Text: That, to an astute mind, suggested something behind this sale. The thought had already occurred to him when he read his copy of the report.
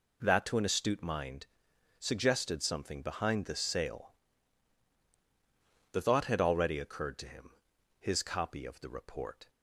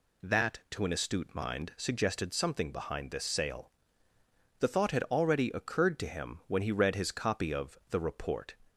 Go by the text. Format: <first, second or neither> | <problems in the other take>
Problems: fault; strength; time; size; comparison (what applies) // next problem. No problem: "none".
second | skips "when he read"; at 7.7 s